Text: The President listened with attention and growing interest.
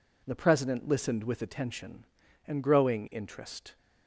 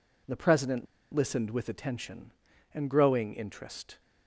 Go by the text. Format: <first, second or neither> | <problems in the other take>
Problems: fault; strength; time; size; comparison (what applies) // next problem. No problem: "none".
first | pauses between "President" and "listened"; slight; at 0.8 s; 0.28 s long